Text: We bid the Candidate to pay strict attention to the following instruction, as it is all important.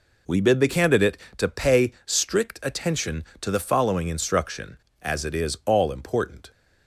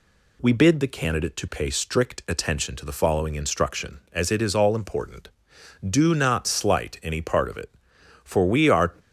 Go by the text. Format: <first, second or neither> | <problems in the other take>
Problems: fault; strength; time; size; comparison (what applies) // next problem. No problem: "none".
first | goes on to say "Do not slight any part of it for we are"; strong; from 5.8 s on; 3.0 s long